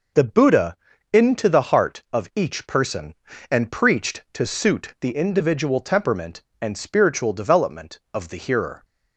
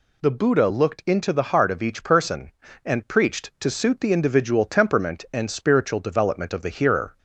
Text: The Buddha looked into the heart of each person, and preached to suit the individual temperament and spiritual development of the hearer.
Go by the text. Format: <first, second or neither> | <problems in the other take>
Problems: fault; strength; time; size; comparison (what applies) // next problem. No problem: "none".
second | skips "looked"; at 0.9 s